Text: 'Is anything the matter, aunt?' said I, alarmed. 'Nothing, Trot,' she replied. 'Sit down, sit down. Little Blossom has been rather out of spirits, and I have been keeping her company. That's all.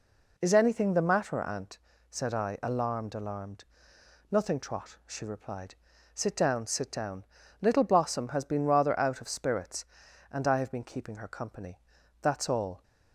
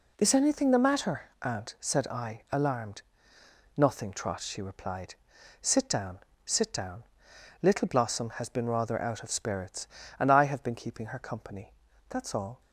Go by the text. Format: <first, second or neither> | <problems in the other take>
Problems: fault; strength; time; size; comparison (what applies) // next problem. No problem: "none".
second | says "alarmed" twice; at 3.1 s